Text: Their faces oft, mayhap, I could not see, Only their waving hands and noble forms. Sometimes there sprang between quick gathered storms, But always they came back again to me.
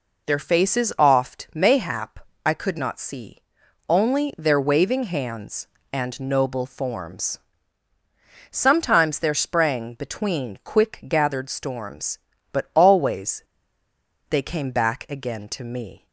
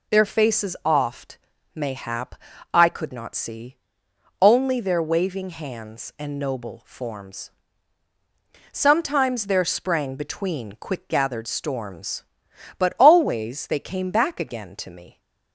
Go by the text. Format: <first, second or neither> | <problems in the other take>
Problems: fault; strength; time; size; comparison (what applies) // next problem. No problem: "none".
second | pauses between "always" and "they"; noticeable; at 13.4 s; 0.88 s long